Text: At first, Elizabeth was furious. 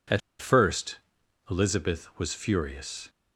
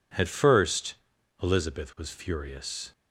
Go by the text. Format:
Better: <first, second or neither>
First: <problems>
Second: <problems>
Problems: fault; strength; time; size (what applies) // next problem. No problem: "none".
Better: second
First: pauses between "At" and "first"; slight; at 0.2 s; 0.21 s long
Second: none